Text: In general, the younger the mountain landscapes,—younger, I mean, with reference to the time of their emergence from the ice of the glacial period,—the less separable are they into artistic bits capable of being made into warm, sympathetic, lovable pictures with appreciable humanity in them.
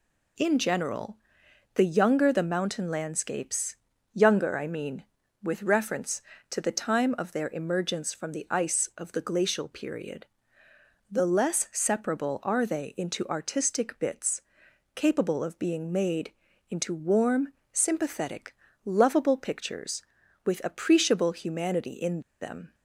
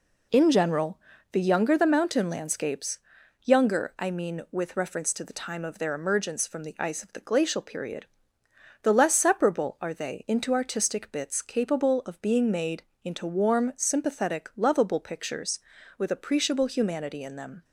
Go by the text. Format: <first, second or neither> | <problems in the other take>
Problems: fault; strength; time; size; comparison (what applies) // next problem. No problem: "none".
second | pauses between "bits" and "capable"; noticeable; at 14.4 s; 0.52 s long // pauses between "made" and "into"; at 16.3 s; 0.38 s long; slight in the second // pauses between "in" and "them"; slight; at 22.1 s; 0.21 s long